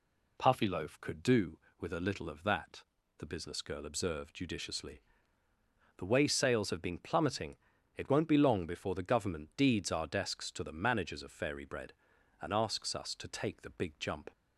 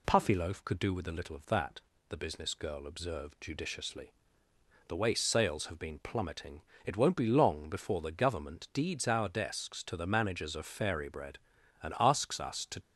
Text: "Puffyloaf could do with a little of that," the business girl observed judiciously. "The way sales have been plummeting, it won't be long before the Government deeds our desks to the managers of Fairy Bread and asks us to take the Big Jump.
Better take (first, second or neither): first